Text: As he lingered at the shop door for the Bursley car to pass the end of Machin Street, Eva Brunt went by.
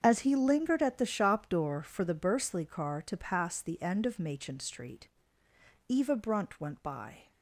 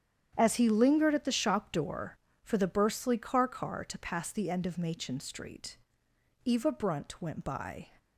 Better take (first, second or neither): first